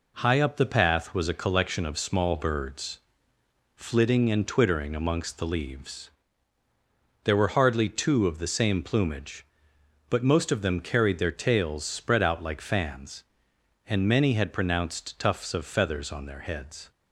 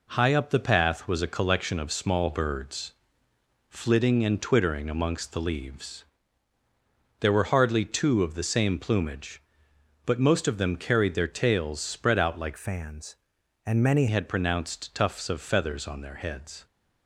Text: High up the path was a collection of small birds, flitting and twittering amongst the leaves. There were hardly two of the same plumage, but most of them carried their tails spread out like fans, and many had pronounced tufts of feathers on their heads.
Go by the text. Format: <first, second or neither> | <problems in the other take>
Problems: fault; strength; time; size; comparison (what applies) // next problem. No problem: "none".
first | changes voice from "fans" to "many"; from 12.5 to 14.0 s; 1.5 s long